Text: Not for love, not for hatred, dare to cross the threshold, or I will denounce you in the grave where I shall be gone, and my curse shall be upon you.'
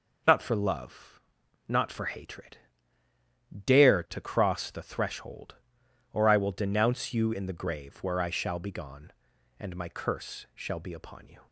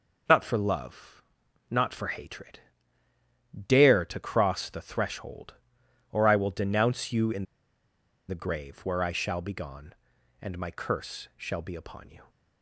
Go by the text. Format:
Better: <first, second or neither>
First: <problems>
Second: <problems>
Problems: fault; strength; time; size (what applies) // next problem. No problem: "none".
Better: first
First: none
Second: pauses between "in" and "the"; noticeable; at 7.4 s; 0.84 s long